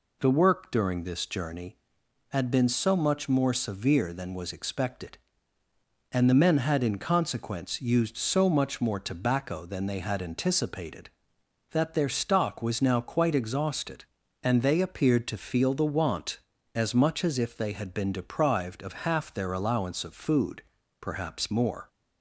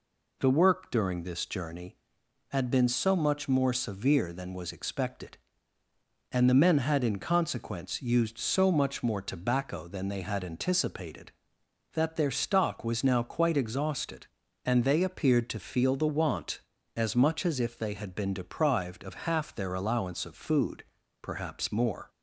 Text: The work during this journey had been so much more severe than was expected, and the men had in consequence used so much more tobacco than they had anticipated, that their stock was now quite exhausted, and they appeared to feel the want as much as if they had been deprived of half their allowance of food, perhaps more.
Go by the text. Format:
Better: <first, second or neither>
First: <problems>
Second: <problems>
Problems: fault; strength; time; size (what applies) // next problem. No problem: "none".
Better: neither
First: none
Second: none